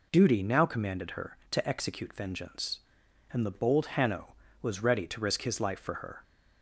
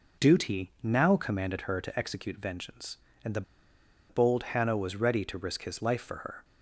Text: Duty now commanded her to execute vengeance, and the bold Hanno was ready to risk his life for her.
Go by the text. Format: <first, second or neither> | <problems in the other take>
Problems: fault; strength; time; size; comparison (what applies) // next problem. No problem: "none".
first | pauses between "the" and "bold"; noticeable; at 3.4 s; 0.67 s long